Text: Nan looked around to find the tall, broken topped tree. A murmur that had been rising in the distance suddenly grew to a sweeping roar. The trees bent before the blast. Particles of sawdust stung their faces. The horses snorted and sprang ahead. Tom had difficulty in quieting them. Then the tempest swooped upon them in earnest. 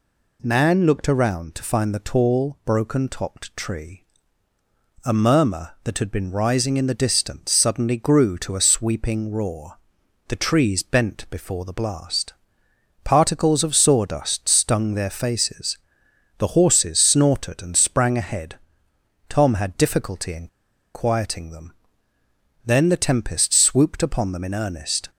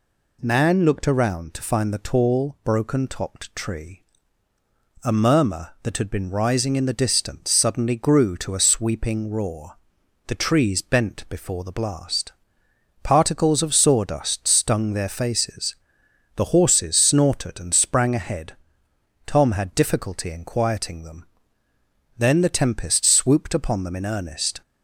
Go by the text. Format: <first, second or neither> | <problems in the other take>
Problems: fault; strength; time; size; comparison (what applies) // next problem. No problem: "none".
second | pauses between "in" and "quieting"; noticeable; at 20.4 s; 0.48 s long